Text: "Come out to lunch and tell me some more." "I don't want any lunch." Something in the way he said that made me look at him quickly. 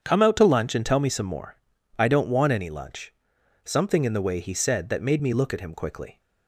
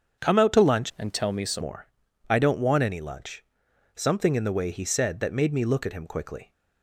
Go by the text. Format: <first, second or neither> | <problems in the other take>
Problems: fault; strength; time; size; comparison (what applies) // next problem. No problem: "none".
first | starts louder than the rest; strong; until 1.3 s; 7.5 dB; strong in the first // changes voice from "and" to "some"; from 0.9 to 1.6 s; 0.7 s long